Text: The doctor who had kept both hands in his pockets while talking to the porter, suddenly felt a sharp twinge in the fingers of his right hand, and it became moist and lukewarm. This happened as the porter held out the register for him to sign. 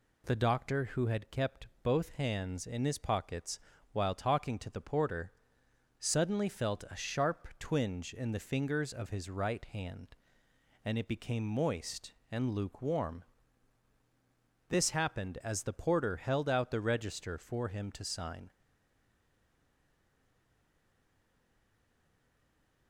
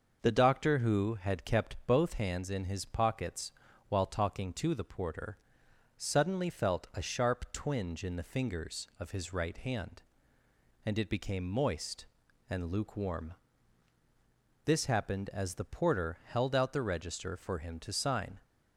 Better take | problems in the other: second | pauses between "kept" and "both"; slight; at 1.6 s; 0.16 s long // pauses between "pockets" and "while"; slight; at 3.5 s; 0.34 s long; slight in the second // stays silent after the last word; strong; from 18.5 s on; 4.3 s long

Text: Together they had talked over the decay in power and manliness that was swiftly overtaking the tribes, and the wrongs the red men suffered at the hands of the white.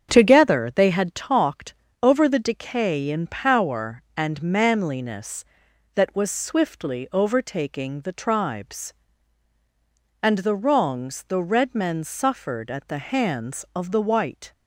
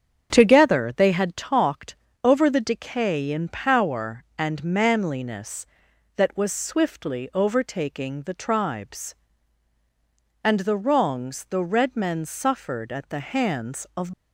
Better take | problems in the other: first | starts louder than the rest; strong; until 1.3 s; 7.5 dB; strong in the first // pauses between "talked" and "over"; slight; at 1.9 s; 0.26 s long; slight in the first // stops before "the white"; at 14.1 s

